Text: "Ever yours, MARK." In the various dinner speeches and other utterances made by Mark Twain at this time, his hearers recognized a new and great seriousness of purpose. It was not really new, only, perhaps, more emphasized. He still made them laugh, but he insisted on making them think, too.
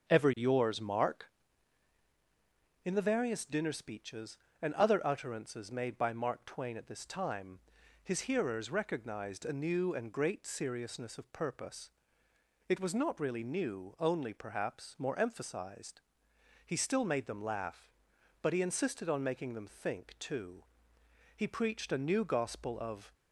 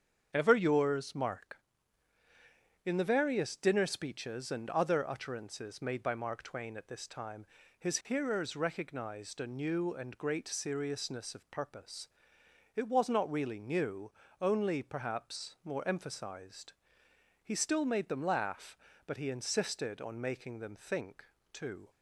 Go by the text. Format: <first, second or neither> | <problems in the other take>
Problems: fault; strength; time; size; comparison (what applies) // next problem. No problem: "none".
second | starts louder than the rest; until 1.1 s; 6.5 dB; strong in the second // goes on to say "He preached a new gospel of"; strong; from 21.3 s on; 1.7 s long